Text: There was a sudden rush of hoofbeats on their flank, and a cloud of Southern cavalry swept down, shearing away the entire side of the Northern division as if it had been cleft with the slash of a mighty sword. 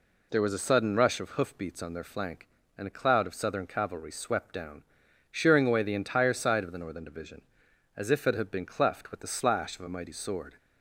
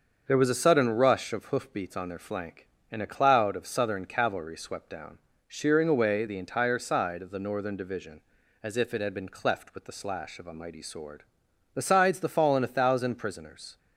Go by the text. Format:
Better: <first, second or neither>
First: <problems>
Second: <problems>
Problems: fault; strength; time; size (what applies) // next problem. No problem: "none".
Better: first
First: none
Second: starts louder than the rest; until 1.2 s; 6.5 dB // goes on to say "Besides the fallen a thousand prisoners"; strong; from 11.7 s on; 2.0 s long